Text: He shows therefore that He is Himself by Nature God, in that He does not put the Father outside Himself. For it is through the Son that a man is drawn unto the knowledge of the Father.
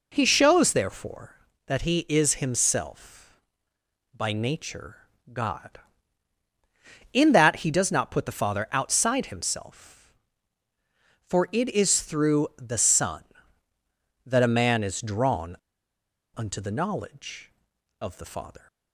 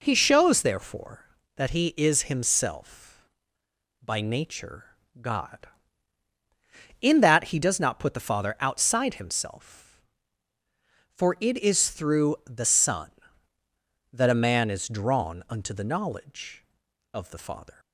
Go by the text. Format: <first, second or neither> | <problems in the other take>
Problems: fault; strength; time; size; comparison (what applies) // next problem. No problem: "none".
second | pauses between "Nature" and "God"; slight; at 4.9 s; 0.36 s long; slight in the second // pauses between "drawn" and "unto"; noticeable; at 15.5 s; 0.80 s long